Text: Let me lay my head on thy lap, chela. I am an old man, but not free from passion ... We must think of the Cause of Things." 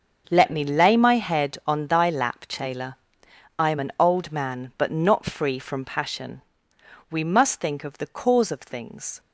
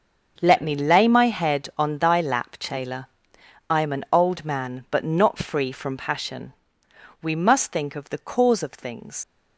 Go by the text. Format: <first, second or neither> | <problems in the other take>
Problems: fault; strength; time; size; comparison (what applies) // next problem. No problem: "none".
first | starts louder than the rest; until 1.4 s; 6.5 dB; also in the first // leaves "Things" unfinished; at 9.2 s; 75 ms